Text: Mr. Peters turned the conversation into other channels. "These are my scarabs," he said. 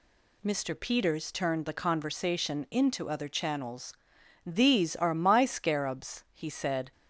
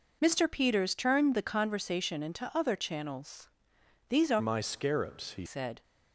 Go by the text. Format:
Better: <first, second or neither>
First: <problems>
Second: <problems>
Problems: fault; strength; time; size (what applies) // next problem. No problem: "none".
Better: first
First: none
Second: changes voice from "my" to "he"; from 4.3 to 5.4 s; 1.1 s long